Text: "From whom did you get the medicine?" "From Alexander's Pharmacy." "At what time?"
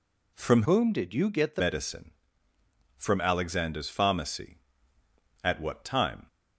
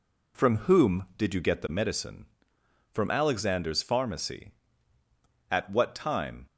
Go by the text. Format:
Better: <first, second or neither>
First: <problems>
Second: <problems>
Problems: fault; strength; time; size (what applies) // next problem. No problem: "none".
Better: second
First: changes voice from "whom" to "the"; from 0.6 to 1.6 s; 1.0 s long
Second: none